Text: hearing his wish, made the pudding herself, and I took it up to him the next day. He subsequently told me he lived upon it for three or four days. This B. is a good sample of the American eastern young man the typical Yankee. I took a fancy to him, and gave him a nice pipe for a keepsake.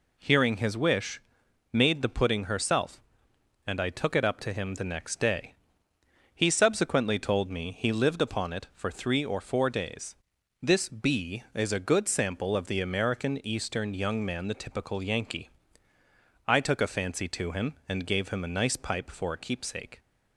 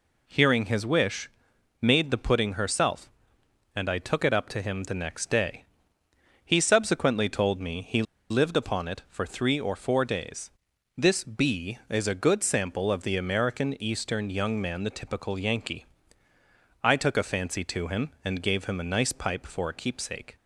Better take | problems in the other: first | pauses between "he" and "lived"; slight; at 8.0 s; 0.27 s long

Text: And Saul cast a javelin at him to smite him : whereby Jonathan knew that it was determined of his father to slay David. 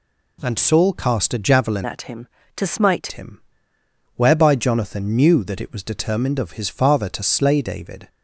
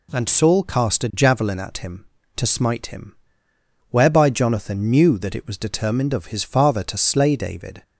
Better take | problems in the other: second | changes voice from "at" to "smite"; from 1.8 to 3.1 s; 1.3 s long

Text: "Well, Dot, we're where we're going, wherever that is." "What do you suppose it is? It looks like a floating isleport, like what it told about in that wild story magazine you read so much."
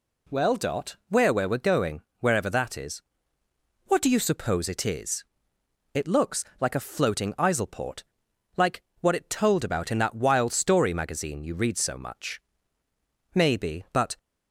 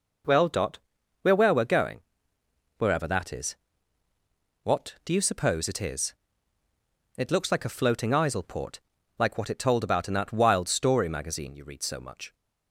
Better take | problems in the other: second | pauses between "looks" and "like"; slight; at 6.4 s; 0.16 s long // pauses between "like" and "what"; slight; at 8.8 s; 0.18 s long // goes on to say "Maybe but"; noticeable; from 13.3 s on; 0.84 s long

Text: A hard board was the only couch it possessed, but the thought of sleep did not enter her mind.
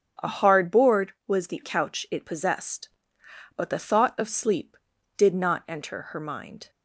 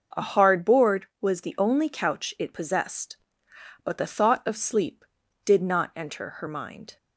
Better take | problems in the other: second | starts louder than the rest; strong; until 1.3 s; 8 dB // skips "only"; at 1.6 s

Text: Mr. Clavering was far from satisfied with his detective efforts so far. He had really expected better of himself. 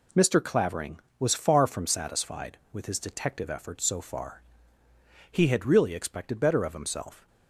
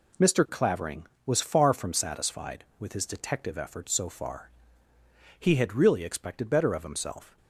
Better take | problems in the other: neither | none

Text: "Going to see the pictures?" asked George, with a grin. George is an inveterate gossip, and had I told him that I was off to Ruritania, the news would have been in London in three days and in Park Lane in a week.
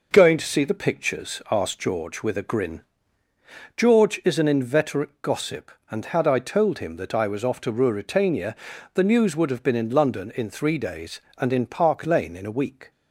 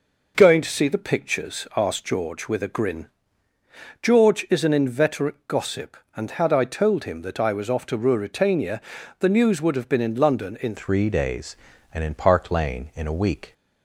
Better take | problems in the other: first | changes voice at "three"; from 10.7 s on; 2.8 s long

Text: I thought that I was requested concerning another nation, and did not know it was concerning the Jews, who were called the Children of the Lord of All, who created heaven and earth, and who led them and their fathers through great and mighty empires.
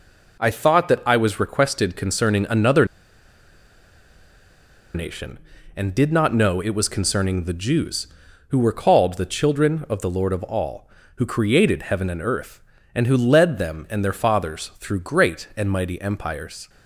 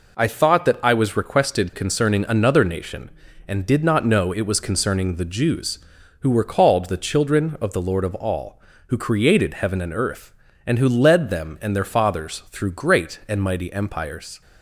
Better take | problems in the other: second | pauses between "another" and "nation"; strong; at 2.8 s; 2.0 s long

